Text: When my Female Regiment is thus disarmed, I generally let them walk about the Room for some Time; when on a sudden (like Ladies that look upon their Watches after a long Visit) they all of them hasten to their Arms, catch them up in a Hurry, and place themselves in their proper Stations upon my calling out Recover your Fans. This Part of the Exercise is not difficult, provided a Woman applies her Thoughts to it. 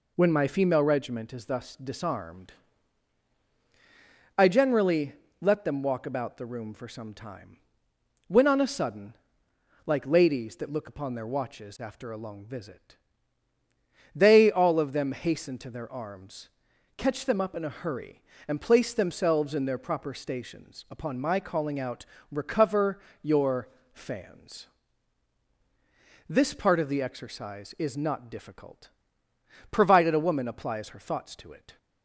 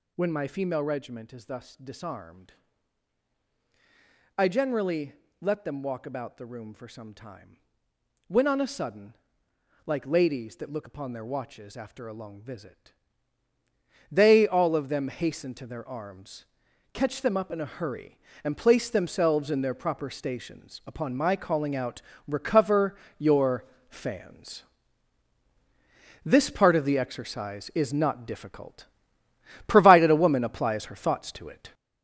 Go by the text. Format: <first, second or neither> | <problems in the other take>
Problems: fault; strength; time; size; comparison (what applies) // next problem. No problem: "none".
first | gets louder; strong; throughout; 7 dB // pauses between "generally" and "let"; slight; at 5.1 s; 0.30 s long; slight in the first // pauses between "out" and "Recover"; slight; at 22.0 s; 0.26 s long; slight in the first // pauses between "Recover" and "your"; slight; at 22.9 s; 0.22 s long; slight in the first // pauses between "your" and "Fans"; slight; at 23.6 s; 0.24 s long; slight in the first